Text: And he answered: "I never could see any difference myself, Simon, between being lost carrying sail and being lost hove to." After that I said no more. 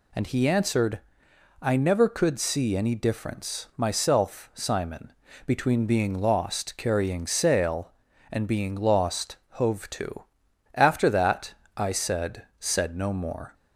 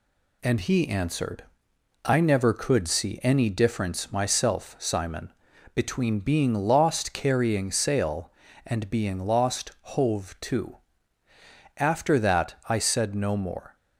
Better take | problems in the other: second | pauses between "that" and "I"; slight; at 11.5 s; 0.24 s long // says "said" twice; at 12.5 s

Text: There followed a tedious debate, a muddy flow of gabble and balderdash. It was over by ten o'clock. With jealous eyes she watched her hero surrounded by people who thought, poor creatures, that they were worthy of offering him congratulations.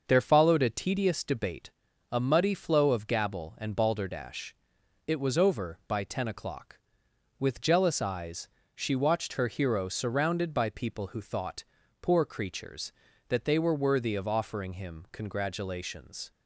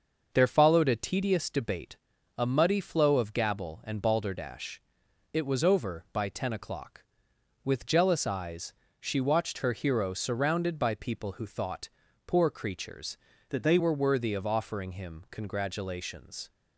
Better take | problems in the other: first | starts louder than the rest; until 1.3 s; 6 dB; also in the first // pauses between "eyes" and "she"; slight; at 8.7 s; 0.26 s long; slight in the first // changes voice from "that" to "they"; from 13.4 to 13.7 s; 0.3 s long

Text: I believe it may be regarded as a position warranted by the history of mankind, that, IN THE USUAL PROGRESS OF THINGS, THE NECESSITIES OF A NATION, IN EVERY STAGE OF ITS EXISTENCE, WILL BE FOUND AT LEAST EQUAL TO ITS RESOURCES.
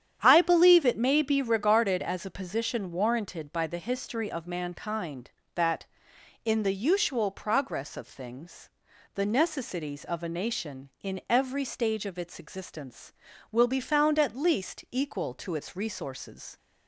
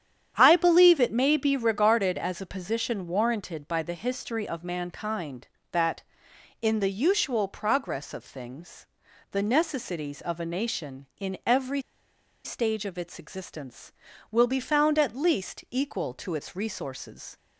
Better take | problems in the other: first | starts louder than the rest; strong; until 1.3 s; 9 dB; strong in the first // pauses between "EVERY" and "STAGE"; noticeable; at 11.8 s; 0.63 s long

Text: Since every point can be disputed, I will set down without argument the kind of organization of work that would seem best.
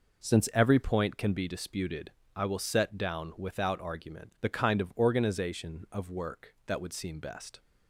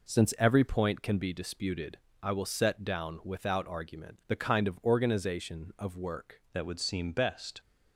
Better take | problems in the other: first | changes voice at "that"; from 6.5 s on; 1.0 s long

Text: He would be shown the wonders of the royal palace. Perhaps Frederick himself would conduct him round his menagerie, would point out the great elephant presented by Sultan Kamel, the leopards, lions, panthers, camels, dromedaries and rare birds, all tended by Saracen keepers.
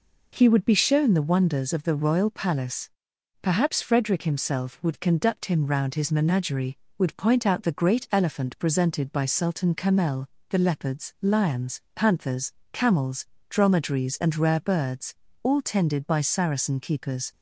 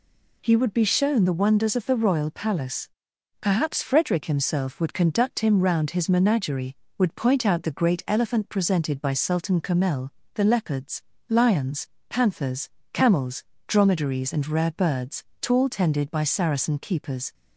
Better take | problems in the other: first | says "tall" for "all"; at 15.4 s

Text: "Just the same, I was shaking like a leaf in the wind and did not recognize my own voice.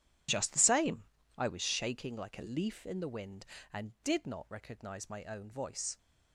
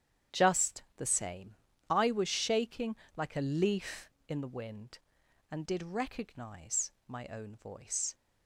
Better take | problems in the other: first | starts louder than the rest; strong; until 1.4 s; 9.5 dB // pauses between "Just" and "the"; slight; at 0.8 s; 0.16 s long // pauses between "shaking" and "like"; slight; at 2.9 s; 0.20 s long // skips "not"; at 5.8 s // pauses between "recognize" and "my"; slight; at 6.9 s; 0.16 s long

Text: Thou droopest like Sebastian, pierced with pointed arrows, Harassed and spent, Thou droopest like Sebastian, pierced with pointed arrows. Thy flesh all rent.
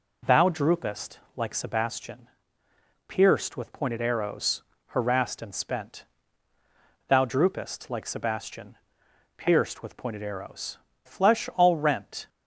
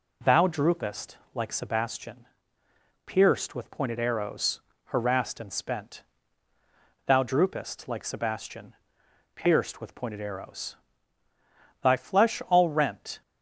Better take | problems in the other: second | pauses between "droopest" and "like"; slight; at 1.1 s; 0.18 s long; slight in the second // skips "Thy"; at 10.9 s

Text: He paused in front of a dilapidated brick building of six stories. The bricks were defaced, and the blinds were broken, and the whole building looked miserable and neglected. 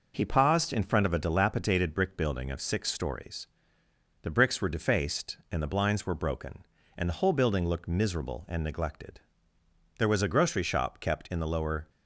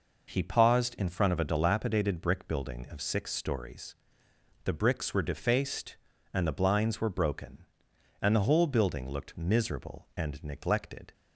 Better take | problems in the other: second | goes on to say "There was a grocery shop kept in the lower"; strong; from 9.9 s on; 1.9 s long

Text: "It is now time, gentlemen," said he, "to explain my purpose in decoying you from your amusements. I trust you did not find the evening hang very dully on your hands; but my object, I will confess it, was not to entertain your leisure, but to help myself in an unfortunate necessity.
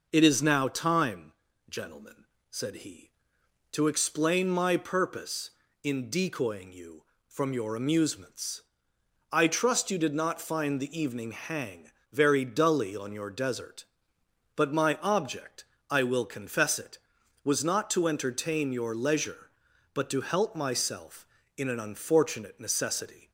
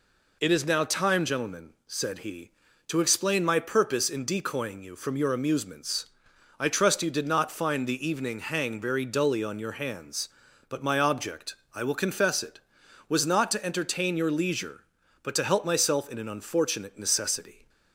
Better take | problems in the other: second | pauses between "hang" and "very"; slight; at 11.9 s; 0.18 s long // says "desert" for "hands"; at 13.2 s

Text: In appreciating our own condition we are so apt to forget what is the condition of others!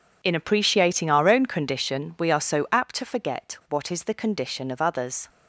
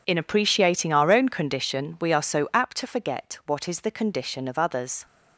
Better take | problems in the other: neither | none

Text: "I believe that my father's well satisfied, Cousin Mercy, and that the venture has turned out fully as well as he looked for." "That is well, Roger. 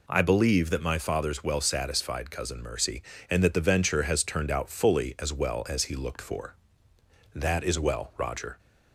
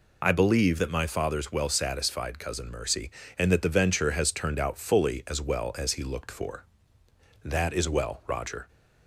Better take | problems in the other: first | loses the start of "I"; at 0.2 s; 35 ms

